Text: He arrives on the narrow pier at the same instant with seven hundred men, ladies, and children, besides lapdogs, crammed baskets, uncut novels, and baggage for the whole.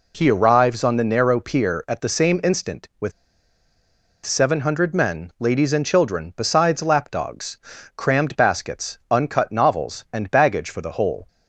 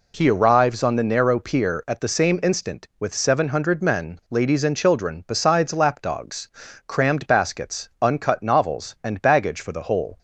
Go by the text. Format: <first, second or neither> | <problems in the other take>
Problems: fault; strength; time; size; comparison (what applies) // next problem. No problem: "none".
second | pauses between "with" and "seven"; at 3.1 s; 1.1 s long